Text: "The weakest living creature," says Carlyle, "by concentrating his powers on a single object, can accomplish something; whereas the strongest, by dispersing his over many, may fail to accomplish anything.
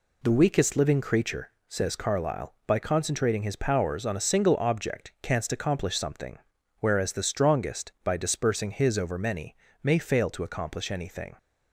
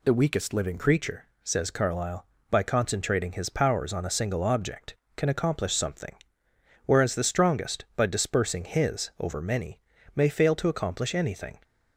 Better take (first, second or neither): second